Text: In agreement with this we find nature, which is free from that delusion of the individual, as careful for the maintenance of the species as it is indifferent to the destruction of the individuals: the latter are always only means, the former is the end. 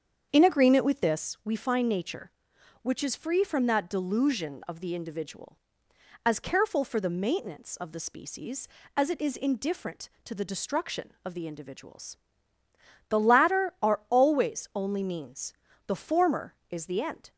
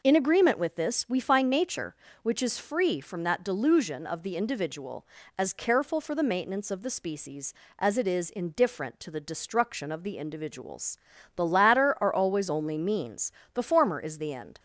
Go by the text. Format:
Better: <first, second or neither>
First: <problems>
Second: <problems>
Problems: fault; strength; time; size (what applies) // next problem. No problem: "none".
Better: second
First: starts louder than the rest; strong; until 1.3 s; 7.5 dB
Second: none